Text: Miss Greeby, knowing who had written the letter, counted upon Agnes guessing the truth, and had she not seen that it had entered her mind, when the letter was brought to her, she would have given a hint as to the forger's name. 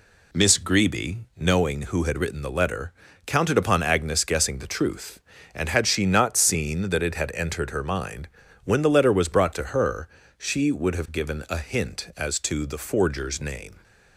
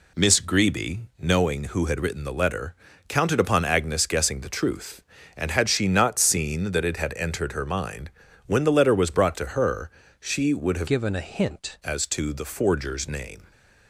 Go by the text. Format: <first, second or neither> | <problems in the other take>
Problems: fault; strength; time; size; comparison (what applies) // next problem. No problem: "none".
first | changes voice from "given" to "hint"; from 10.8 to 11.7 s; 0.9 s long